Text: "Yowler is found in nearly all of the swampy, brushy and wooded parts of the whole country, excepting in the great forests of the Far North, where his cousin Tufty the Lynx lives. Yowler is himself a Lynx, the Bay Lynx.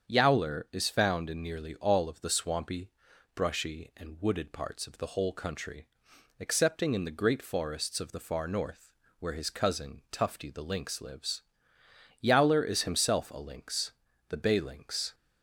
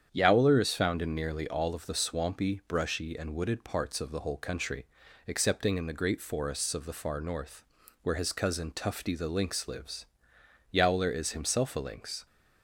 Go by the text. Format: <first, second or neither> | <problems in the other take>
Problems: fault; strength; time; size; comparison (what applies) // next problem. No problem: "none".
first | starts louder than the rest; strong; until 1.1 s; 8.5 dB; strong in the first // stops before "the Bay Lynx"; at 12.2 s